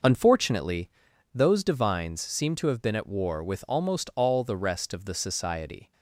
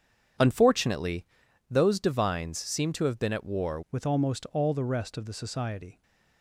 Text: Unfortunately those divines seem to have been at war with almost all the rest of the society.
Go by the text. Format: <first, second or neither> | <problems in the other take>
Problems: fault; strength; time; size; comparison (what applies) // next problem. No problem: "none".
first | starts louder than the rest; strong; until 1.8 s; 8 dB // pauses between "Unfortunately" and "those"; at 1.2 s; 0.44 s long; also in the first // changes voice at "with"; from 3.9 s on; 2.1 s long